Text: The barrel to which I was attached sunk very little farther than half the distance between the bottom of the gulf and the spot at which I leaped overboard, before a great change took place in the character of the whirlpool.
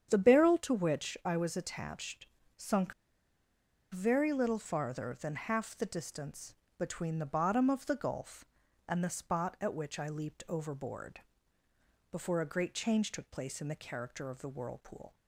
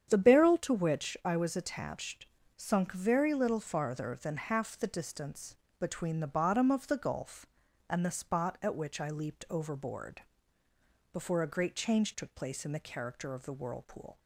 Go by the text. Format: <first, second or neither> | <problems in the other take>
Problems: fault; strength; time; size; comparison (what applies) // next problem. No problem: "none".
second | starts louder than the rest; strong; until 1.1 s; 8.5 dB; strong in the second // pauses between "attached" and "sunk"; slight; at 2.2 s; 0.32 s long; slight in the second // pauses between "sunk" and "very"; at 2.9 s; 0.98 s long // pauses between "distance" and "between"; slight; at 6.5 s; 0.24 s long; slight in the second